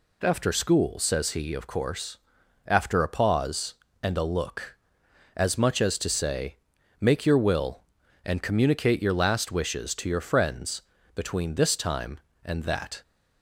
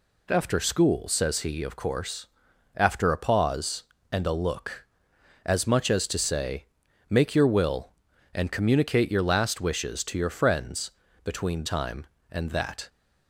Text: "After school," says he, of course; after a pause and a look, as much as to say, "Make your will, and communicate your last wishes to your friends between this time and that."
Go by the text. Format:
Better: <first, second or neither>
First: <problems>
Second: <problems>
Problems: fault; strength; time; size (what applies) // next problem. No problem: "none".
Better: first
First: pauses between "friends" and "between"; slight; at 10.8 s; 0.34 s long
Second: pauses between "friends" and "between"; slight; at 10.9 s; 0.34 s long // skips "this"; at 11.6 s